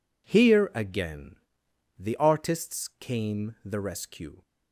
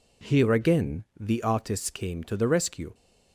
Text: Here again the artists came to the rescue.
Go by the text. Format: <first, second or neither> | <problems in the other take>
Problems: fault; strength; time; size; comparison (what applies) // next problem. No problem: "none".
second | pauses between "again" and "the"; noticeable; at 1.3 s; 0.62 s long; slight in the second // skips "to"; at 3.5 s